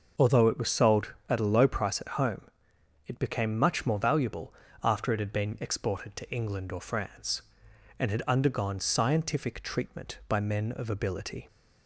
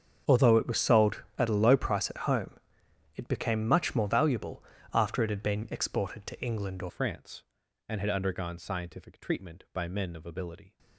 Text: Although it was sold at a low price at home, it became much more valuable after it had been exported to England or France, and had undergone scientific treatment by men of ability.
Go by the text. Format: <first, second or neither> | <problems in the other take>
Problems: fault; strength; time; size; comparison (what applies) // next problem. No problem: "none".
first | starts louder than the rest; strong; until 1.4 s; 7.5 dB // pauses between "valuable" and "after"; slight; at 4.6 s; 0.32 s long; slight in the first // changes voice at "France"; from 6.8 s on; 3.9 s long